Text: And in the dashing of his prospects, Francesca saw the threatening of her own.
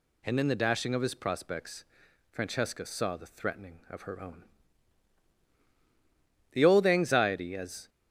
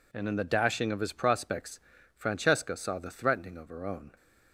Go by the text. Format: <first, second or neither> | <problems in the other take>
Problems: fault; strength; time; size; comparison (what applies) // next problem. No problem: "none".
second | goes on to say "The old anxiety as"; from 6.5 s on; 1.3 s long